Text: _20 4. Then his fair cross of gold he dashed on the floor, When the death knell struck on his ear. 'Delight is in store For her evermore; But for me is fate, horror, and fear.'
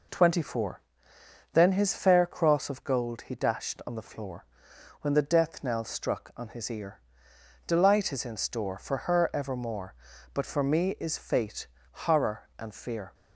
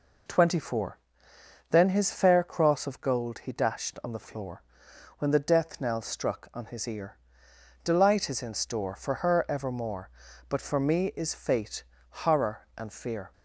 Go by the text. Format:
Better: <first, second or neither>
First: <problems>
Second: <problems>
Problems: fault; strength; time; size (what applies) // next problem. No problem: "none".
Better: neither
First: none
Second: none